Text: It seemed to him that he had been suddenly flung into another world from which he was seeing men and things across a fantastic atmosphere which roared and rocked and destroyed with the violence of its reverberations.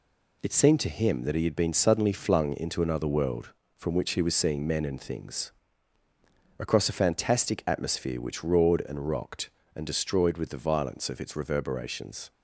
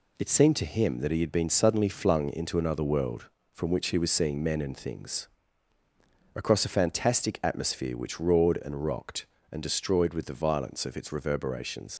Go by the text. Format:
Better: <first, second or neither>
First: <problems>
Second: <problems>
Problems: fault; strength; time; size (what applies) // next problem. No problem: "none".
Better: first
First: pauses between "things" and "across"; at 5.5 s; 1.1 s long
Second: pauses between "things" and "across"; at 5.2 s; 1.1 s long // leaves "reverberations" unfinished; at 11.9 s; 100 ms